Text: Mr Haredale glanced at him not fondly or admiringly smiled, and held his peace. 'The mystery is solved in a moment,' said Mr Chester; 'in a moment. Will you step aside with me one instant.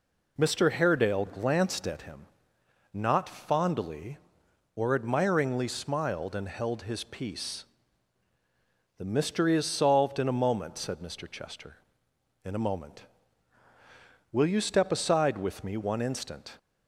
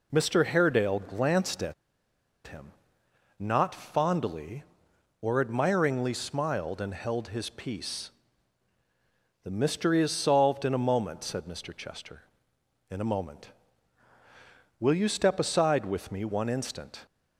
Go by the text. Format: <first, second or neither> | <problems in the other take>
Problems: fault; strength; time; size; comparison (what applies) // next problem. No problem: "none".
first | pauses between "at" and "him"; noticeable; at 1.7 s; 0.73 s long // pauses between "him" and "not"; noticeable; at 2.7 s; 0.66 s long; noticeable in the first